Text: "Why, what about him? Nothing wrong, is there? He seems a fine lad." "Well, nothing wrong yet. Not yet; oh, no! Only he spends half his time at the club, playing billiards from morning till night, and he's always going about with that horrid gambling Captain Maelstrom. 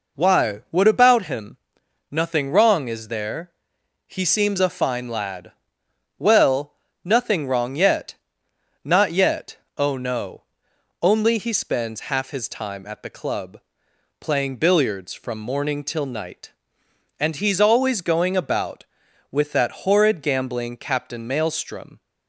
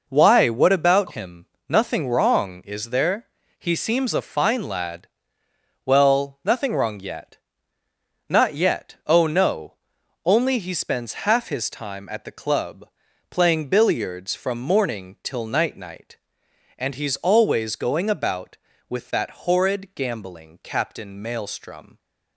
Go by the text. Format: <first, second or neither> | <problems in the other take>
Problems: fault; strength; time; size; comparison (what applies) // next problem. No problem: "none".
first | says "night" twice; at 15.7 s